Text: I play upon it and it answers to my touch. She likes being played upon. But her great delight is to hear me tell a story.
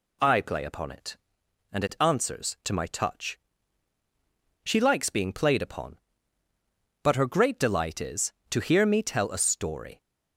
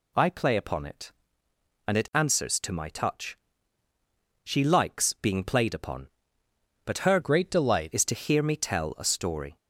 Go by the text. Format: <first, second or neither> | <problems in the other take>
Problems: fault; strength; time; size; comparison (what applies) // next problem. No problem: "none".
first | changes voice from "great" to "delight"; from 7.2 to 7.9 s; 0.7 s long